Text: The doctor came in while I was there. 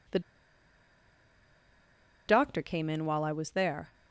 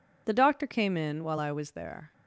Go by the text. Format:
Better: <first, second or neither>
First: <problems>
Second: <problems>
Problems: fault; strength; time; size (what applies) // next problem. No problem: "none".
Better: second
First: pauses between "The" and "doctor"; strong; at 0.1 s; 2.0 s long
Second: none